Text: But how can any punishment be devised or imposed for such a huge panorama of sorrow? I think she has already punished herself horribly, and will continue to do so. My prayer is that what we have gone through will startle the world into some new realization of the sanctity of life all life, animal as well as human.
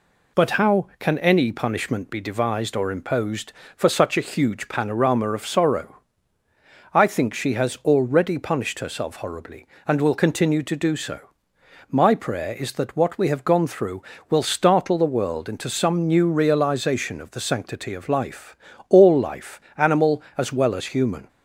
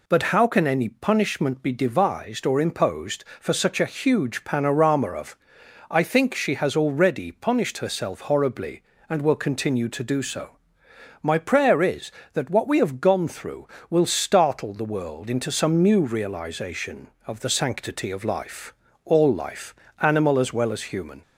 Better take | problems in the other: first | skips "sorrow"; at 5.6 s // pauses between "life" and "all"; slight; at 18.7 s; 0.30 s long; slight in the first

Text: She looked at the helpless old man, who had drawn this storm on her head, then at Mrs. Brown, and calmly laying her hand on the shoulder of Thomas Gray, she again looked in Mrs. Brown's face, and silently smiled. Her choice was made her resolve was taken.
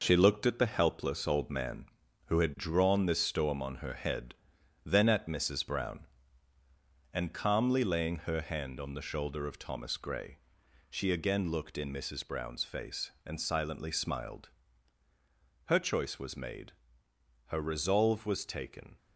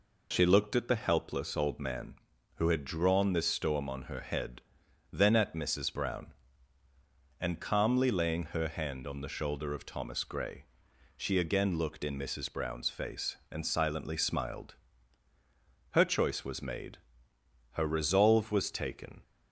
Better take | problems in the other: second | gets quieter; noticeable; throughout; 5.5 dB // pauses between "made" and "her"; noticeable; at 16.7 s; 0.74 s long; noticeable in the second

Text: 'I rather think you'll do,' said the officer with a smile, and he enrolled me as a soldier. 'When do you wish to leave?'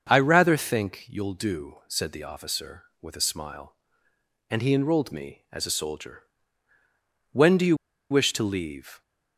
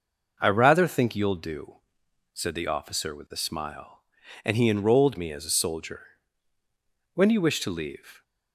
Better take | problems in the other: second | starts louder than the rest; until 1.1 s; 6.5 dB // pauses between "you" and "wish"; slight; at 7.7 s; 0.34 s long

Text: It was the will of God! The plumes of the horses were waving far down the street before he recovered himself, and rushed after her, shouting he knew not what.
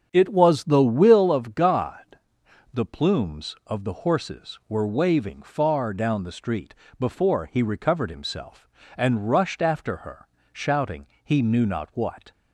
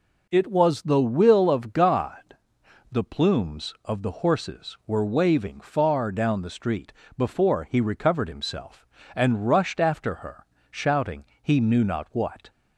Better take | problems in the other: second | starts louder than the rest; strong; until 1.3 s; 7.5 dB // pauses between "street" and "before"; slight; at 6.7 s; 0.26 s long; slight in the second // pauses between "shouting" and "he"; slight; at 11.0 s; 0.18 s long; slight in the second

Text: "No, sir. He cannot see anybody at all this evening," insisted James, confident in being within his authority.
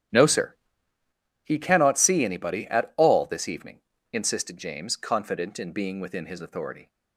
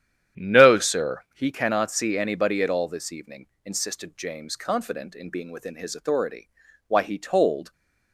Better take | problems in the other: first | starts louder than the rest; strong; until 1.5 s; 10 dB; strong in the first // goes on to say "Why he told"; noticeable; from 6.8 s on; 0.84 s long

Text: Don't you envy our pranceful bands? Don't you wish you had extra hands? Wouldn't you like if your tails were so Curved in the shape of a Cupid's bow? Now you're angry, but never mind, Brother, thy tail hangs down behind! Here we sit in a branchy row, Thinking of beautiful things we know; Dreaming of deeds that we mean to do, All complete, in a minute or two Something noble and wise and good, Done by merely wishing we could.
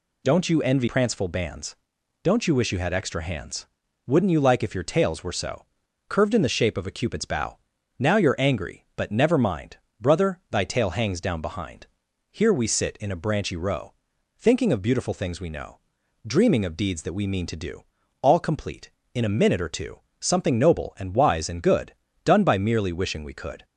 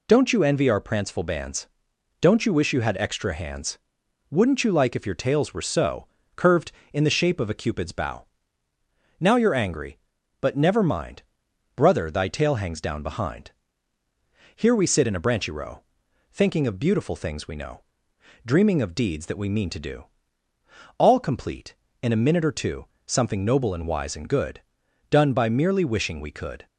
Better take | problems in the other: second | skips "our"; at 0.8 s // pauses between "so" and "Curved"; at 5.6 s; 0.42 s long; slight in the second // pauses between "two" and "Something"; slight; at 19.9 s; 0.22 s long; slight in the second

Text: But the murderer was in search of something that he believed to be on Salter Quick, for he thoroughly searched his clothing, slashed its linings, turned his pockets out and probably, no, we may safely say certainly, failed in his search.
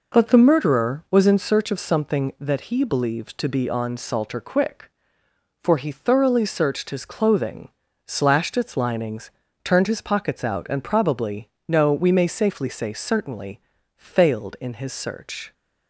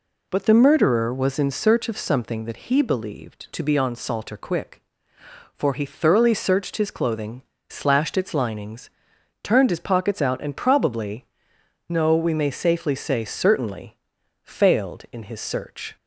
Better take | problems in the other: neither | none

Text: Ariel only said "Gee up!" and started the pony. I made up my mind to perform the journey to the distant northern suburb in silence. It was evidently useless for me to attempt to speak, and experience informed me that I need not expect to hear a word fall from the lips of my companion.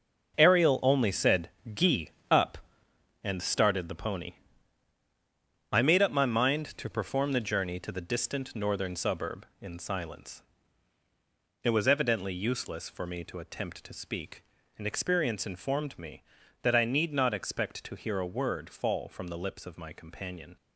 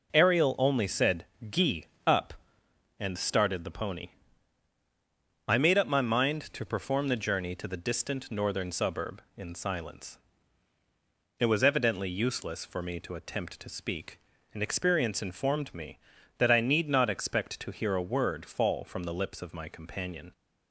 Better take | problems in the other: second | gets quieter; strong; throughout; 10.5 dB // pauses between "said" and "Gee"; slight; at 1.5 s; 0.22 s long; slight in the second // pauses between "Gee" and "up"; slight; at 2.1 s; 0.18 s long; slight in the second

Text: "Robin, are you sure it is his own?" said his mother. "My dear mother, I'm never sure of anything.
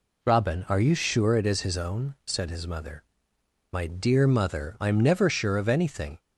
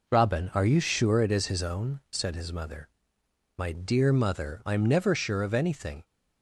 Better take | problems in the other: first | gets quieter; noticeable; throughout; 5.5 dB

